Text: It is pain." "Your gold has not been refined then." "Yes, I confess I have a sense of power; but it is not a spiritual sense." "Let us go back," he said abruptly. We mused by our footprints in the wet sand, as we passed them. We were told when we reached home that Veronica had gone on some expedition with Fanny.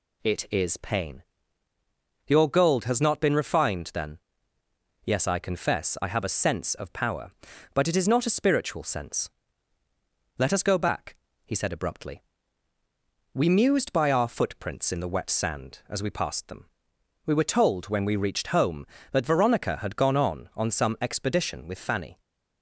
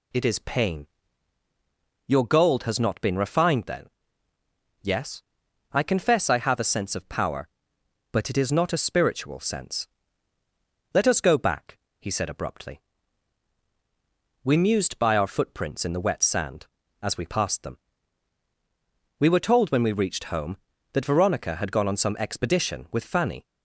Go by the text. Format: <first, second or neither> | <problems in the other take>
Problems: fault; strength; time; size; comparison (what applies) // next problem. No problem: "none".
second | says "on" twice; at 20.5 s